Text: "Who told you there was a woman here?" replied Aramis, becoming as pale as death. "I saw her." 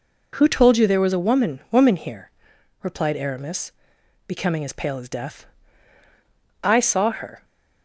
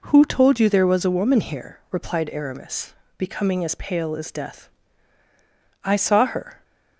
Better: second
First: says "woman" twice; at 1.6 s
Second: none

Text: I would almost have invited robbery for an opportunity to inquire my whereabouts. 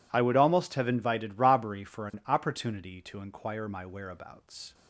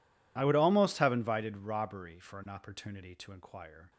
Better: first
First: none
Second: stops before "my whereabouts"; at 3.9 s

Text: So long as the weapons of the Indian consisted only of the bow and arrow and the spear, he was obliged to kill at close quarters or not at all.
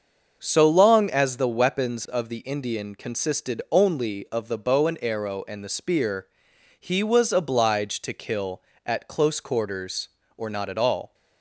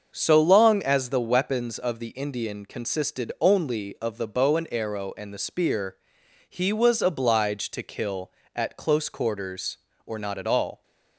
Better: neither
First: starts louder than the rest; until 1.4 s; 6.5 dB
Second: starts louder than the rest; until 1.1 s; 6.5 dB

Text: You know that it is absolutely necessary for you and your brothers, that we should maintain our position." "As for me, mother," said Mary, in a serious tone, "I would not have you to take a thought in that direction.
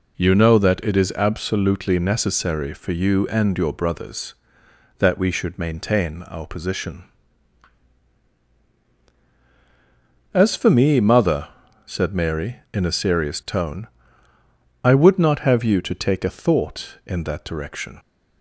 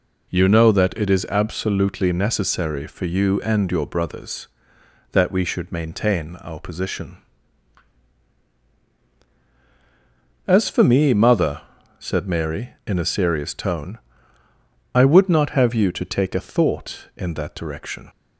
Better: neither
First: none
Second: none

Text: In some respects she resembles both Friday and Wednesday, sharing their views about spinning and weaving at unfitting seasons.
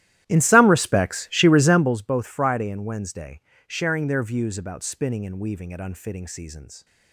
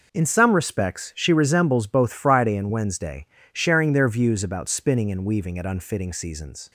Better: second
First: starts louder than the rest; strong; until 2.0 s; 13.5 dB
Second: none

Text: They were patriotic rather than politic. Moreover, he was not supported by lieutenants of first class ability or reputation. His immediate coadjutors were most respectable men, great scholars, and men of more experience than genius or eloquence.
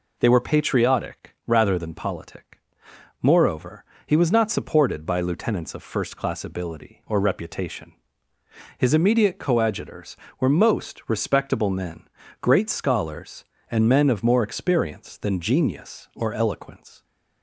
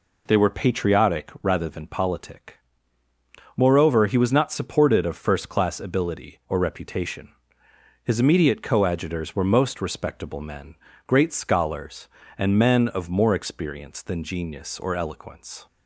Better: first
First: none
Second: skips "by lieutenants"; at 5.0 s

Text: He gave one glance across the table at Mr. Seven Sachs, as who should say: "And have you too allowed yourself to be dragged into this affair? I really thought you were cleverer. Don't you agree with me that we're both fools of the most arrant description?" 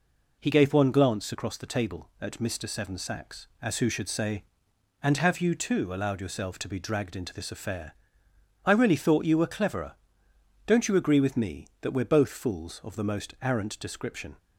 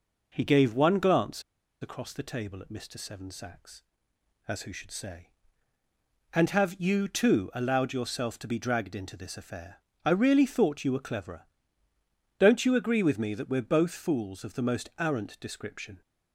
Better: first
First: none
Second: pauses between "glance" and "across"; at 1.4 s; 0.39 s long

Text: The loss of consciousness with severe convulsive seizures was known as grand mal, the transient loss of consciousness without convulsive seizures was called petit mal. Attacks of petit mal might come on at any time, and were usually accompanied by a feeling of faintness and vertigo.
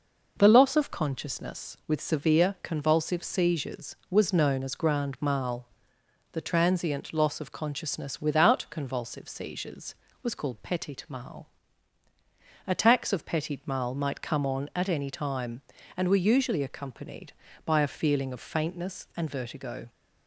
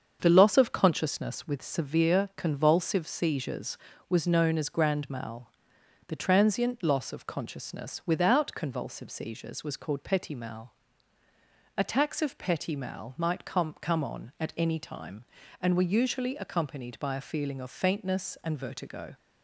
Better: first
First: none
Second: starts louder than the rest; until 1.2 s; 7 dB // says "come" twice; at 13.8 s

